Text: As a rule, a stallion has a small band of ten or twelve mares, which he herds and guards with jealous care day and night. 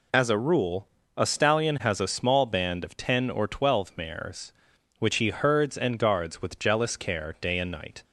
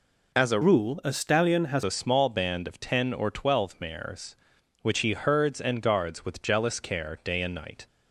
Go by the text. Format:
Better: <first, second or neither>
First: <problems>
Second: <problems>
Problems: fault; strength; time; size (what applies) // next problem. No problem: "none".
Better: first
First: none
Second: changes voice from "rule" to "has"; from 0.6 to 1.8 s; 1.2 s long